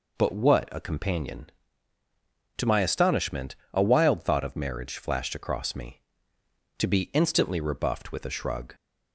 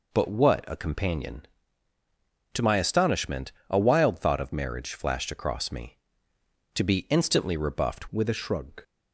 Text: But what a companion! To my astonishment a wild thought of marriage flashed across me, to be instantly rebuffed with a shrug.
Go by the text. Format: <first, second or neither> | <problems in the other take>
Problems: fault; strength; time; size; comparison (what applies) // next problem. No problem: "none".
first | pauses between "astonishment" and "a"; slight; at 3.5 s; 0.18 s long; slight in the first // changes voice at "with"; from 8.1 s on; 0.7 s long